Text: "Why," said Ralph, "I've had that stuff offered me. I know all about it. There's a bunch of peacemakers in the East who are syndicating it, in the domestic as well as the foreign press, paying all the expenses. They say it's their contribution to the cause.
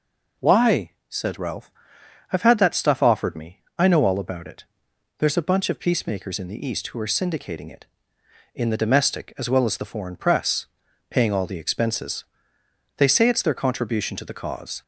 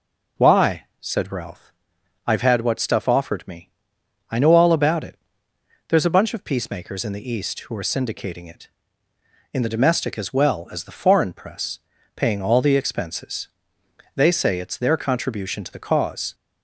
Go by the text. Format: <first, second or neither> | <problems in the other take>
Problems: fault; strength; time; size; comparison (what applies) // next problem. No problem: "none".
first | says "what" for "that"; at 2.6 s